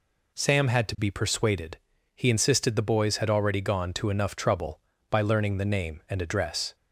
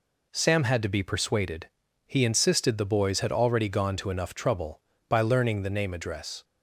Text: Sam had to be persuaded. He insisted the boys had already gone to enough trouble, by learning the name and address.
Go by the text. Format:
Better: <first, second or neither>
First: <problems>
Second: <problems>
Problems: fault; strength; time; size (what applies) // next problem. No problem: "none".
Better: first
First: none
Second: skips "and"; at 5.9 s